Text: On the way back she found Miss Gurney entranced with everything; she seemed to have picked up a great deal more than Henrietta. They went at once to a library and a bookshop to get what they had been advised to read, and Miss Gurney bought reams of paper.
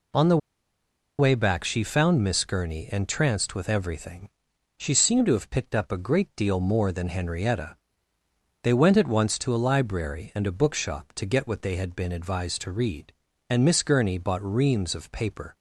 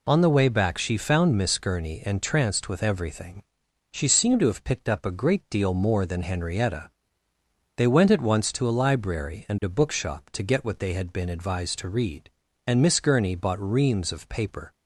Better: second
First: pauses between "the" and "way"; noticeable; at 0.3 s; 0.81 s long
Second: none

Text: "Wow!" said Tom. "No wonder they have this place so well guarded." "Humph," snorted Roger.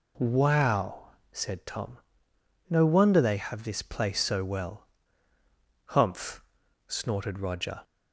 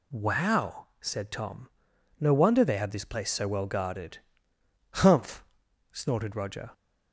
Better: second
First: skips "guarded"; at 5.3 s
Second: none

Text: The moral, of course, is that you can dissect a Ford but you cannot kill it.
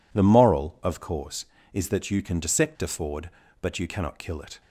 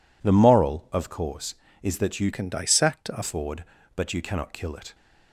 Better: first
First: none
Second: changes voice from "can" to "a"; from 2.3 to 3.2 s; 0.9 s long

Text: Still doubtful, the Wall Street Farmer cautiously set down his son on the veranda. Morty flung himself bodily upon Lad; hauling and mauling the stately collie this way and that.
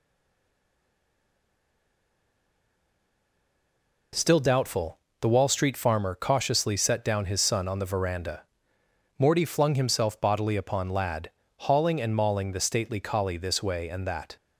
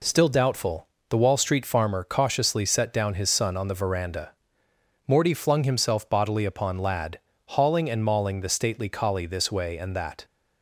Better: second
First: stays silent before the first word; strong; until 4.1 s; 4.1 s long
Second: none

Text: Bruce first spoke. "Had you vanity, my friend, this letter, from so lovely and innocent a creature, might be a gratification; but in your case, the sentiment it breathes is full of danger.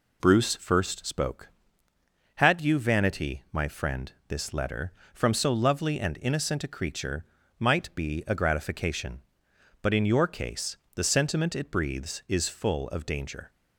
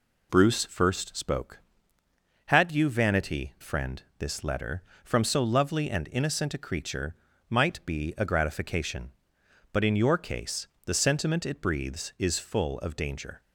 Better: first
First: none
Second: skips "my"; at 3.5 s

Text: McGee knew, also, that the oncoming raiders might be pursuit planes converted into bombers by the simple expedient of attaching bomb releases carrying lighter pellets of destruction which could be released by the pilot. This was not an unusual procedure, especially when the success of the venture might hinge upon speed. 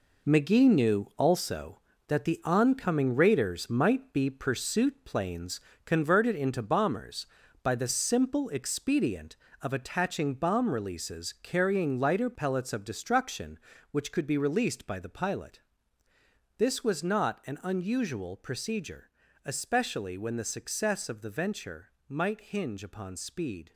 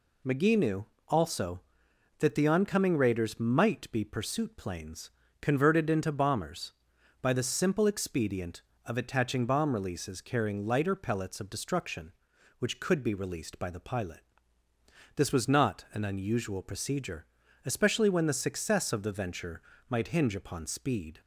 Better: second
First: gets quieter; strong; throughout; 8.5 dB // pauses between "planes" and "converted"; slight; at 5.5 s; 0.26 s long // pauses between "venture" and "might"; slight; at 21.9 s; 0.16 s long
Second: pauses between "planes" and "converted"; slight; at 5.1 s; 0.30 s long // pauses between "venture" and "might"; slight; at 19.6 s; 0.26 s long

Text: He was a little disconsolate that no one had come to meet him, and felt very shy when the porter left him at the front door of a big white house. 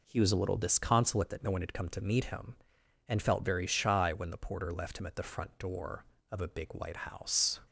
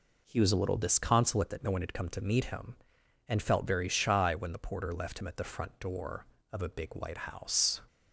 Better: neither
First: none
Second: none

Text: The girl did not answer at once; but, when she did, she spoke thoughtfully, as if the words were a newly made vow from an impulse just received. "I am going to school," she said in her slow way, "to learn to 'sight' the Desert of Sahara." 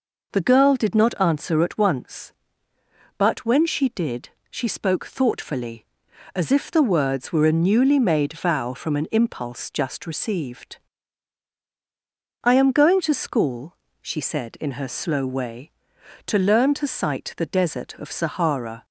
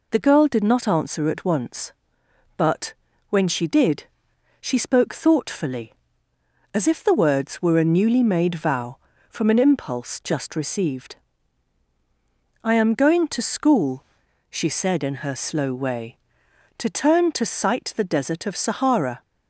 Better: first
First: none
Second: says "turn" for "learn"; at 16.8 s

